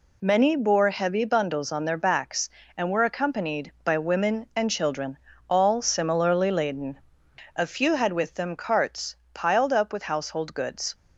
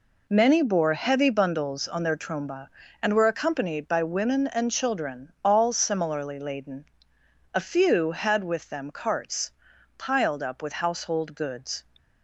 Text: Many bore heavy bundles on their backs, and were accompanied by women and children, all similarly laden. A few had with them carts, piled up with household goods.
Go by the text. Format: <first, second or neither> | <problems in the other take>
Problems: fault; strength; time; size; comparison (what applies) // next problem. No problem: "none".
first | says "tromba" for "backs"; at 2.1 s